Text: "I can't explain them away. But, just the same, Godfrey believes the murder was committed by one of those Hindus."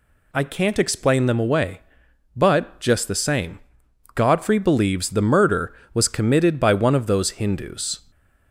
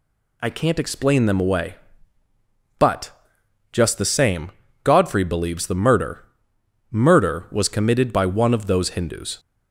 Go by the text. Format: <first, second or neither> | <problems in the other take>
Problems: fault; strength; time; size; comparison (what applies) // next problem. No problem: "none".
first | says "murder" twice; at 6.9 s